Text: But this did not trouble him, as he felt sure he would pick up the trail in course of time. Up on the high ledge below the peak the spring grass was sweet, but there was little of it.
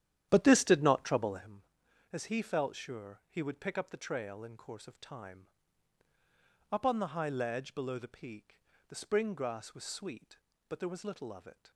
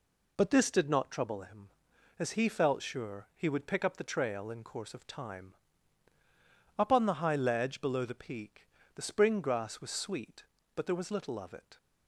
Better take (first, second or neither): second